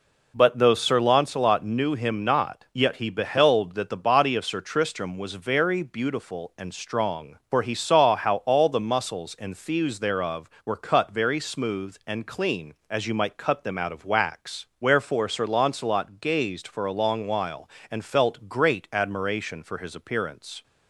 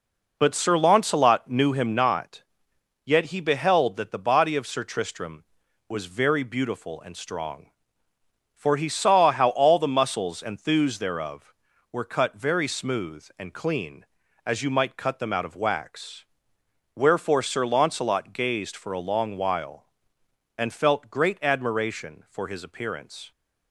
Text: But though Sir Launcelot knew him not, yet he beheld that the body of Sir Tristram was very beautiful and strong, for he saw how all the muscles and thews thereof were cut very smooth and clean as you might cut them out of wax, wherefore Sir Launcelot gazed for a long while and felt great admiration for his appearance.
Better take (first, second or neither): first